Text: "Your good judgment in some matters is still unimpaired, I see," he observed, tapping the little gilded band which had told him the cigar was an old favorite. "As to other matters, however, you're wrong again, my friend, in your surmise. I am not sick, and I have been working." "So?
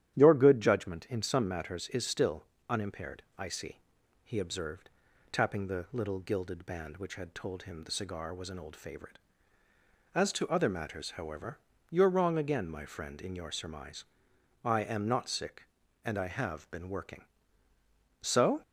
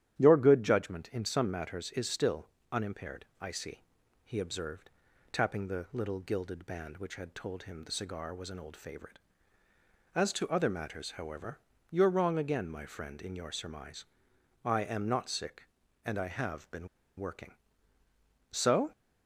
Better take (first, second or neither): first